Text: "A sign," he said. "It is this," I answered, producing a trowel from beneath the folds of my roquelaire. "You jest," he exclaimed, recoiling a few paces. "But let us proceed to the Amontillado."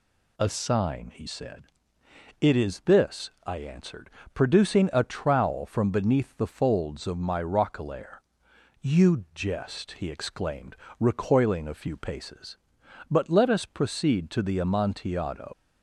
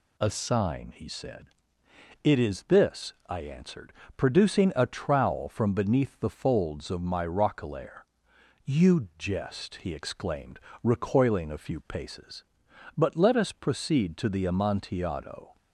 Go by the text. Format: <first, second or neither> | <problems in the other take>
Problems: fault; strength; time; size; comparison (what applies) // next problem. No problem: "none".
second | leaves "Amontillado" unfinished; at 15.5 s; 160 ms